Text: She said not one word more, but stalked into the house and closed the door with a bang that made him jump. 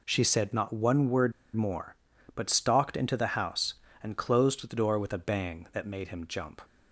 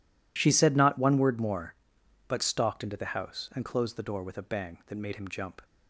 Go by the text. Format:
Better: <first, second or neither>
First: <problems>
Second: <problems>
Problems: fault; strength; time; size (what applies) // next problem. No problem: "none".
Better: second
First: pauses between "word" and "more"; slight; at 1.3 s; 0.22 s long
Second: none